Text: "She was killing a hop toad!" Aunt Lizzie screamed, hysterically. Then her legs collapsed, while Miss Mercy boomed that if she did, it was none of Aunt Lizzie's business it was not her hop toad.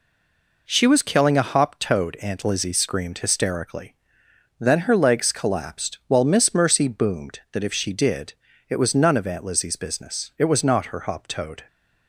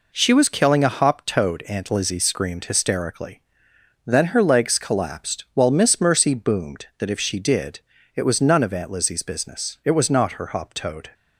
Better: second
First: stays silent before the first word; slight; until 0.6 s; 0.6 s long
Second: none

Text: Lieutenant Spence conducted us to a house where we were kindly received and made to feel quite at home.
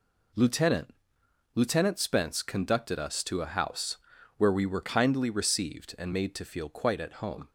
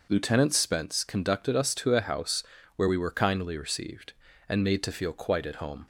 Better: second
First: says "Lieutenant" twice; at 1.5 s // pauses between "house" and "where"; at 3.9 s; 0.40 s long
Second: pauses between "house" and "where"; slight; at 2.4 s; 0.34 s long

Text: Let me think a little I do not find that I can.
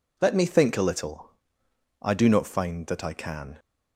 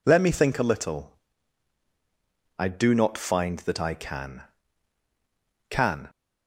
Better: first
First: pauses between "little" and "I"; noticeable; at 1.2 s; 0.72 s long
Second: pauses between "little" and "I"; strong; at 1.1 s; 1.4 s long // says "can" twice; at 5.6 s

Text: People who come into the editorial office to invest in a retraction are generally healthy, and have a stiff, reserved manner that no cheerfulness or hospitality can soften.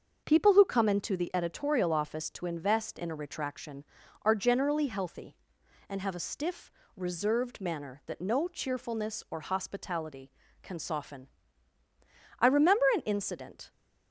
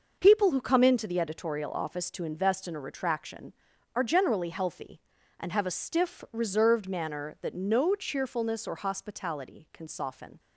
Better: second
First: starts louder than the rest; until 1.2 s; 6.5 dB // goes on to say "I remember an incident"; from 12.3 s on; 1.3 s long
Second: none

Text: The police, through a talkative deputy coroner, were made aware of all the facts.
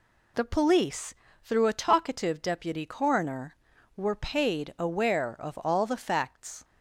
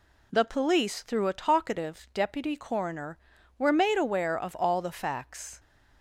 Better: second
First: says "paid" for "made"; at 4.1 s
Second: none

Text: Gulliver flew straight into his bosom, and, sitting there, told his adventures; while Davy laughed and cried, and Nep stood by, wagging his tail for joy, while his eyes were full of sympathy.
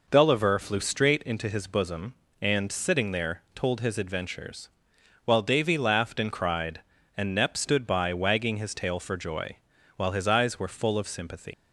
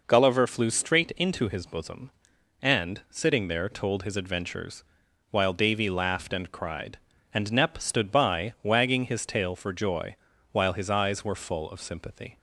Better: second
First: leaves "sympathy" unfinished; at 11.5 s; 135 ms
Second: none

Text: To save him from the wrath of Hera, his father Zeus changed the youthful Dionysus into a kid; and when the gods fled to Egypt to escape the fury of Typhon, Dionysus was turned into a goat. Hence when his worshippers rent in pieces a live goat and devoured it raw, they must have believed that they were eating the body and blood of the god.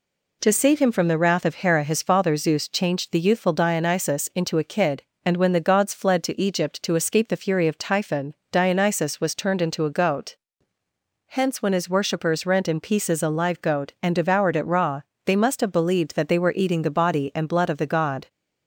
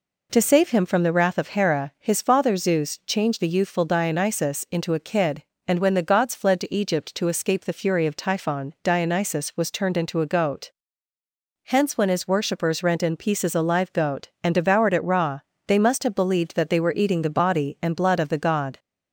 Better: neither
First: none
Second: none

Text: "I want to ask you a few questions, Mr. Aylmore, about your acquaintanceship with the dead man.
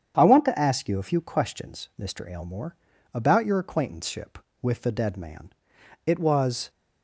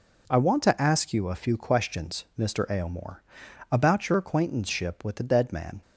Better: second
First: starts louder than the rest; strong; until 1.1 s; 8.5 dB // goes on to say "It was"; noticeable; from 6.0 s on; 0.64 s long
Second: none

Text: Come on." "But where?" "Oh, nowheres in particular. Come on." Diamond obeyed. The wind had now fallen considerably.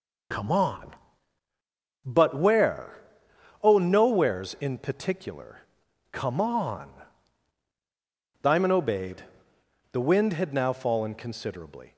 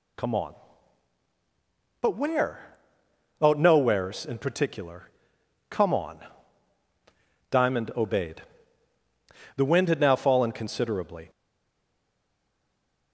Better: first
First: none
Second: stays silent after the last word; noticeable; from 11.2 s on; 1.9 s long

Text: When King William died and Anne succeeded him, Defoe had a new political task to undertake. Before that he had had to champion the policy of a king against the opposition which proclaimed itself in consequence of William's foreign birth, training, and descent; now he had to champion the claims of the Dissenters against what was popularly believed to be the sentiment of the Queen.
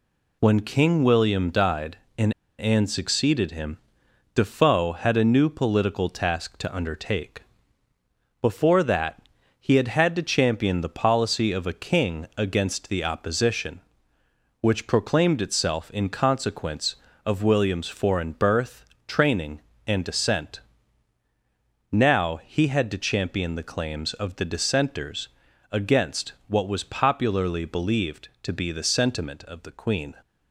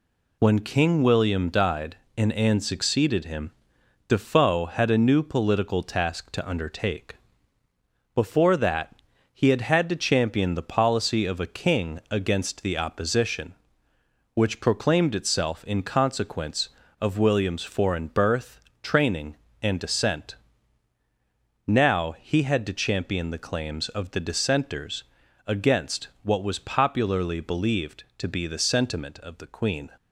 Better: second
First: pauses between "and" and "Anne"; slight; at 2.3 s; 0.25 s long // pauses between "that" and "he"; at 9.2 s; 0.40 s long // pauses between "Dissenters" and "against"; at 25.2 s; 0.42 s long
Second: pauses between "that" and "he"; at 8.9 s; 0.40 s long // pauses between "Dissenters" and "against"; at 25.0 s; 0.42 s long

